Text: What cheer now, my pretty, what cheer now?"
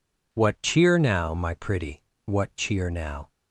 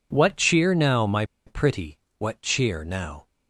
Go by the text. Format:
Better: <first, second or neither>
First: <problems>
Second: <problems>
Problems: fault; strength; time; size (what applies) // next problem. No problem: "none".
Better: first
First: none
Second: pauses between "my" and "pretty"; slight; at 1.2 s; 0.23 s long